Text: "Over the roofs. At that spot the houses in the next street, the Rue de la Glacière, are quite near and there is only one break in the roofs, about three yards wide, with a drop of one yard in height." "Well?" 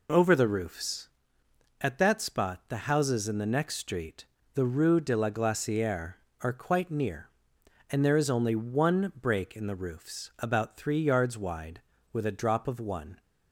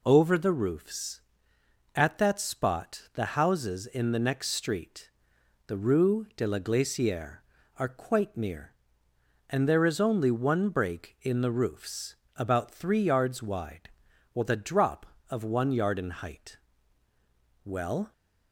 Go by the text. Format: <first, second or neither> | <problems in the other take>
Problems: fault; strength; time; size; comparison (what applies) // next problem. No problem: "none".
second | stops before "yard in height Well"; at 13.2 s